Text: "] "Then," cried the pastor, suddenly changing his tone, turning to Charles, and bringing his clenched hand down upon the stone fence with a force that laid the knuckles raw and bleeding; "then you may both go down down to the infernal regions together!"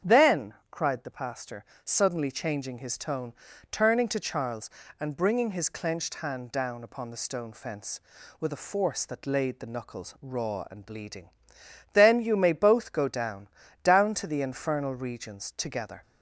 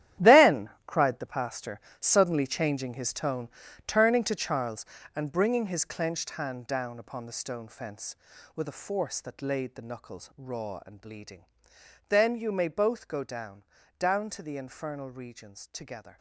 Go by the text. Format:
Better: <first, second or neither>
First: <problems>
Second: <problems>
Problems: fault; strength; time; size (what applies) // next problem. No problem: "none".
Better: first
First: starts louder than the rest; strong; until 1.2 s; 8 dB // pauses between "down" and "down"; slight; at 13.4 s; 0.34 s long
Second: gets quieter; strong; throughout; 13 dB // starts louder than the rest; strong; until 1.3 s; 11.5 dB // pauses between "down" and "down"; slight; at 13.6 s; 0.34 s long